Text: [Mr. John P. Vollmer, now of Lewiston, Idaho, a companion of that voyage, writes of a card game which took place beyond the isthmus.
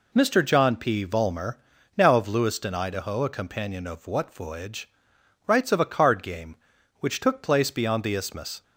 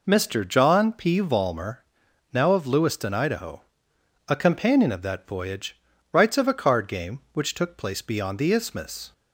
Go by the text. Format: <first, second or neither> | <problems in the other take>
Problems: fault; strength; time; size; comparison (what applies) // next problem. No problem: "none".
second | says "what" for "that"; at 4.0 s